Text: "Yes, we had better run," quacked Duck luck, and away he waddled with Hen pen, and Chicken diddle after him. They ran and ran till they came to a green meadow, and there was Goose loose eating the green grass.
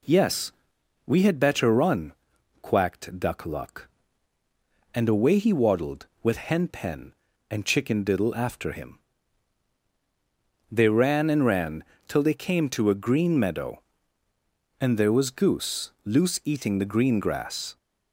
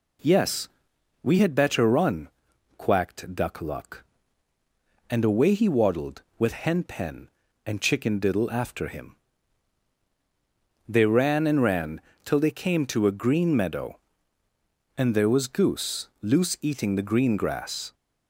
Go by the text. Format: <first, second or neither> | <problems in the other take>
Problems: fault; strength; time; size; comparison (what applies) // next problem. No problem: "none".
neither | pauses between "ran" and "till"; slight; the same in both